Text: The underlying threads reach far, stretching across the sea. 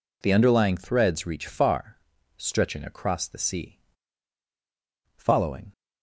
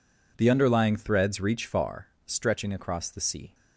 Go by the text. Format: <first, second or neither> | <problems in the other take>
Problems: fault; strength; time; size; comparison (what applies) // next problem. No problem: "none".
second | goes on to say "Following"; from 5.1 s on; 0.54 s long